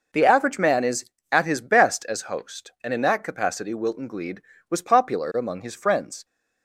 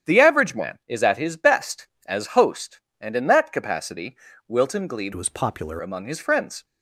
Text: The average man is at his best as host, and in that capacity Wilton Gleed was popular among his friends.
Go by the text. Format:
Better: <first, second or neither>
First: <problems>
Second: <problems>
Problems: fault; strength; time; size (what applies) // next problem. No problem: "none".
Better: first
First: none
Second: starts louder than the rest; strong; until 1.1 s; 9 dB // pauses between "capacity" and "Wilton"; slight; at 4.1 s; 0.30 s long // changes voice from "was" to "popular"; from 5.1 to 5.7 s; 0.6 s long